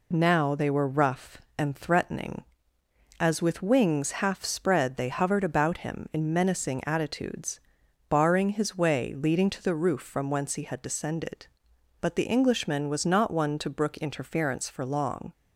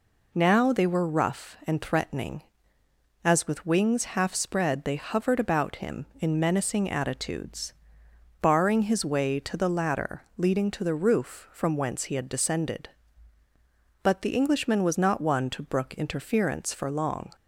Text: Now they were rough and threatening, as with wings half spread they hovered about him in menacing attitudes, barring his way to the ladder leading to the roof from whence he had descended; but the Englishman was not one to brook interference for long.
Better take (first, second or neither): second